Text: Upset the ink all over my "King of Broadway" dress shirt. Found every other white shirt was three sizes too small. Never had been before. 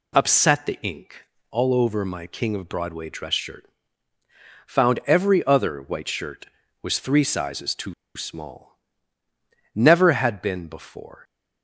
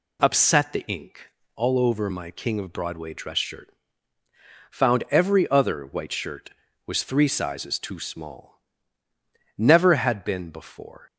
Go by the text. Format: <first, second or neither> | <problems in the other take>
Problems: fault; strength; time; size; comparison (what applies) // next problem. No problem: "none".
second | pauses between "ink" and "all"; slight; at 1.2 s; 0.26 s long; slight in the second // pauses between "too" and "small"; slight; at 7.9 s; 0.23 s long